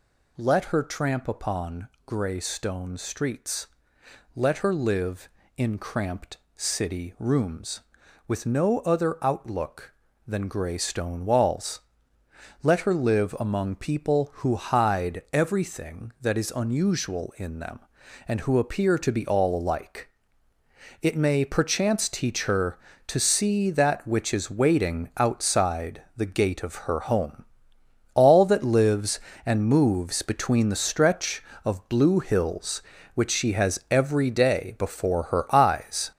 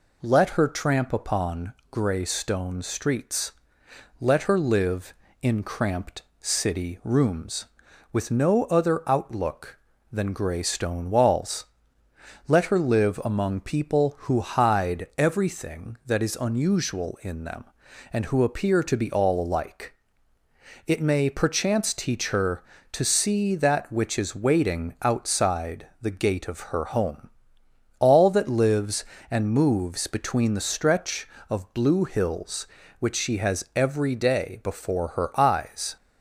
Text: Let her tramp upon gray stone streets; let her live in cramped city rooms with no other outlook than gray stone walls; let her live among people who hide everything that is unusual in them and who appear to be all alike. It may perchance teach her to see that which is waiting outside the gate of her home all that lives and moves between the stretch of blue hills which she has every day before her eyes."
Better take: second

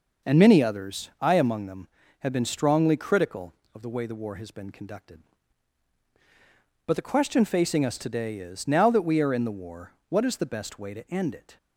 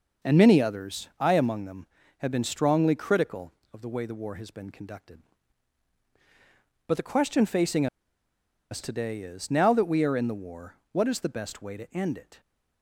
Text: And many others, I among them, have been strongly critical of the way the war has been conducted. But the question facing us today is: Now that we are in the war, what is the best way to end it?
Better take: first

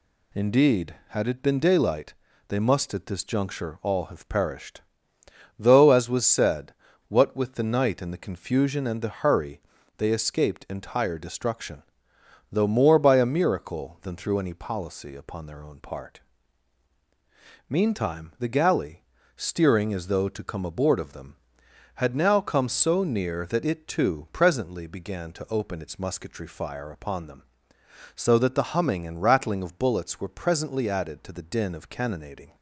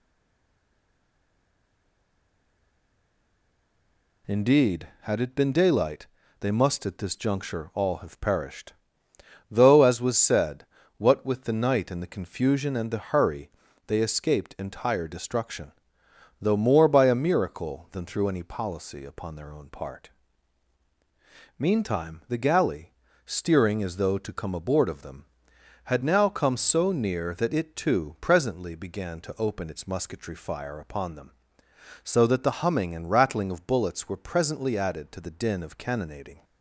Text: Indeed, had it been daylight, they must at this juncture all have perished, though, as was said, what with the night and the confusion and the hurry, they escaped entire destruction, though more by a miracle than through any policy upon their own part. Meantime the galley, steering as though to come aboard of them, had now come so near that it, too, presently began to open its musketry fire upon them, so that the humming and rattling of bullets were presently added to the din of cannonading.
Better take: first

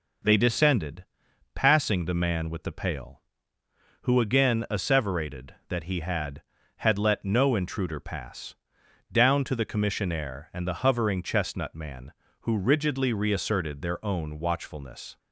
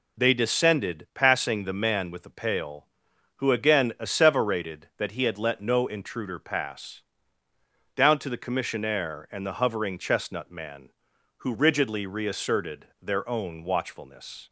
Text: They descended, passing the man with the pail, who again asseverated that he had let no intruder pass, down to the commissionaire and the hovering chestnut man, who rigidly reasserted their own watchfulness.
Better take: second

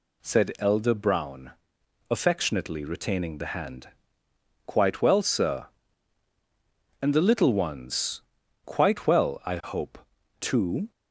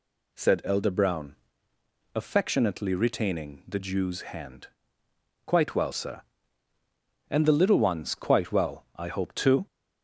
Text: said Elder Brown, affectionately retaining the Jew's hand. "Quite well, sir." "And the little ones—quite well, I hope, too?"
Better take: second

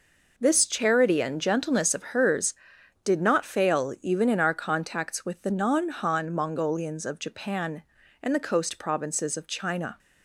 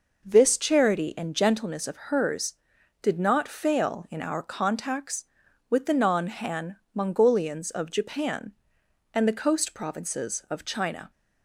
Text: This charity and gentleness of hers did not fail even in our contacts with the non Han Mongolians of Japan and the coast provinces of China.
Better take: first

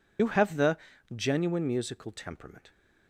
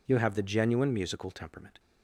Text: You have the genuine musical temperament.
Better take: second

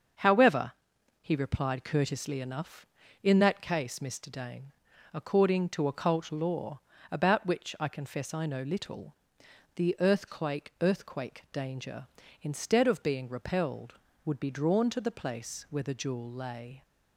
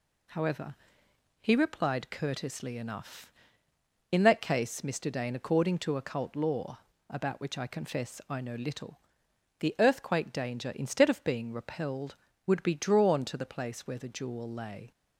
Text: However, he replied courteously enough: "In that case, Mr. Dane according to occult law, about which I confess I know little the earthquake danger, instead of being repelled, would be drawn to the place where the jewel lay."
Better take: second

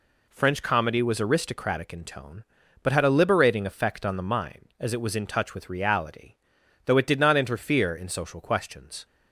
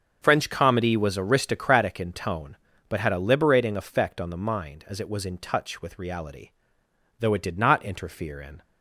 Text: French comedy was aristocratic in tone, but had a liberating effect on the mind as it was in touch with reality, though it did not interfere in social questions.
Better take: first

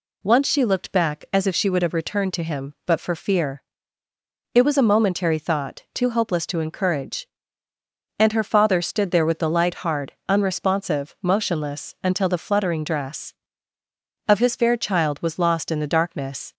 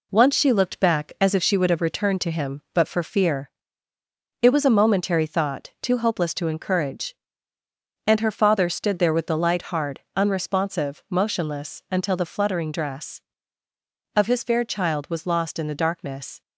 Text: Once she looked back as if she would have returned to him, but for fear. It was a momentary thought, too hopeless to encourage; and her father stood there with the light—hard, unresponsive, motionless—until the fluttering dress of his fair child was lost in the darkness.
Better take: first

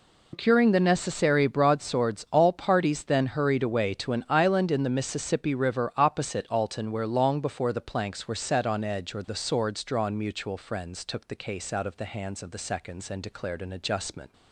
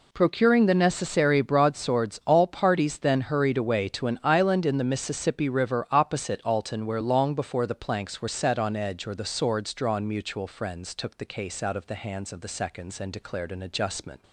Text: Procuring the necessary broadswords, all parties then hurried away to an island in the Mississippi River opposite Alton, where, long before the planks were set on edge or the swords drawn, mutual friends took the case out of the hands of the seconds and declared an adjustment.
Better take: second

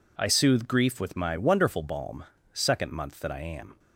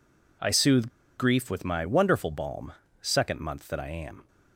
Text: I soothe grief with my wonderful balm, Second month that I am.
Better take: first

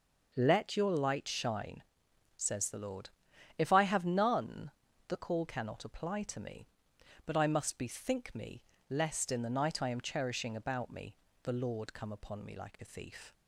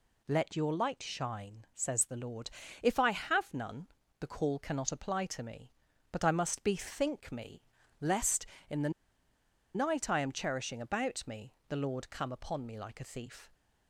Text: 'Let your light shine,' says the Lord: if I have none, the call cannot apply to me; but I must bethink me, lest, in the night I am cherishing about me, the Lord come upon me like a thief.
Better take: first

